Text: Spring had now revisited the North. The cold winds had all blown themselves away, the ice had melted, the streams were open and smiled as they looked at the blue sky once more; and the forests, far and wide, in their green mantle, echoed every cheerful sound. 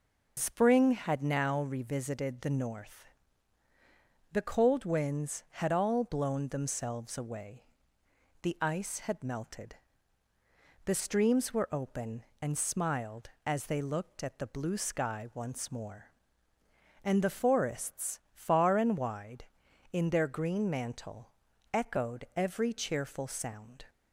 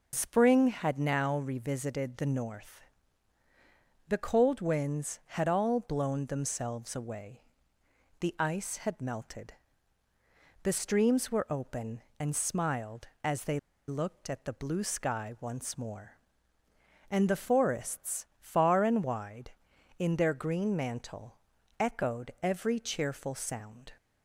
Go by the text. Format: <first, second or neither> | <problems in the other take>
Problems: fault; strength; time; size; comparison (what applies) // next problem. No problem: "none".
first | pauses between "they" and "looked"; slight; at 13.5 s; 0.30 s long